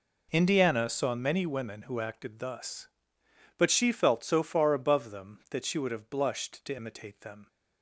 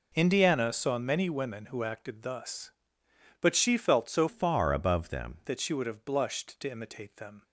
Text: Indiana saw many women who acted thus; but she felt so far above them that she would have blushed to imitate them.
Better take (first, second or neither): first